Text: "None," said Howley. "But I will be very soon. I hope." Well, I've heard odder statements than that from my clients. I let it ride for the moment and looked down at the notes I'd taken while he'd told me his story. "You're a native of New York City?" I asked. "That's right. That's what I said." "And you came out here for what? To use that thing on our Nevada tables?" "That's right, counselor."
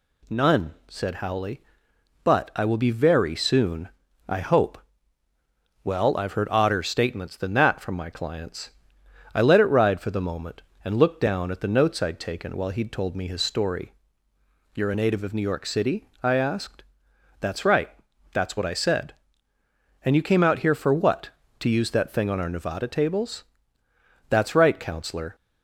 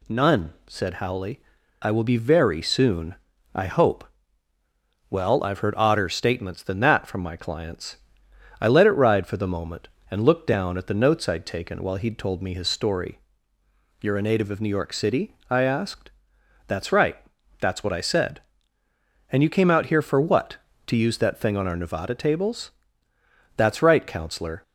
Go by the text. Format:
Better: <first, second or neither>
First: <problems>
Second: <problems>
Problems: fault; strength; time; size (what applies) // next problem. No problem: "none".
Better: first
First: none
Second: skips "But"; at 1.6 s